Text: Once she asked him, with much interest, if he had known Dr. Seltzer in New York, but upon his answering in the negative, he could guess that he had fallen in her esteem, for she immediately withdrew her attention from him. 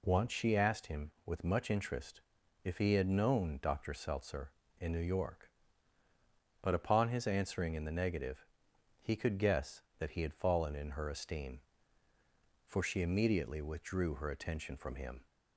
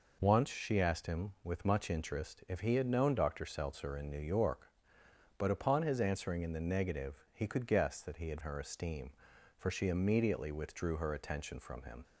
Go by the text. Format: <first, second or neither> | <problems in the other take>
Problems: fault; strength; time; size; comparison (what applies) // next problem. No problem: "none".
first | skips "fallen in"; at 8.4 s